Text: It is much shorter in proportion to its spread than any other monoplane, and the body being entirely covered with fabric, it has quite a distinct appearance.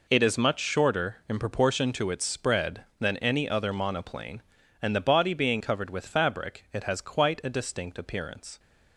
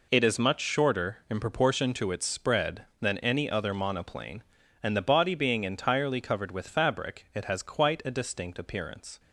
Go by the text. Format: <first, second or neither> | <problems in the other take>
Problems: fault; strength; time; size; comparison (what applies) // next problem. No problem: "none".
second | skips "entirely"; at 5.6 s